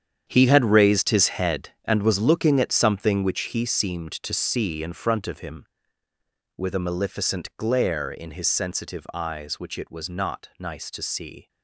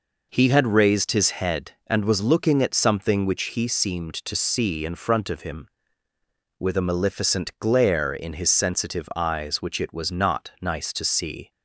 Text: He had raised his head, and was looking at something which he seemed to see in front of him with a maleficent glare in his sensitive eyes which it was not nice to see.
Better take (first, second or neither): second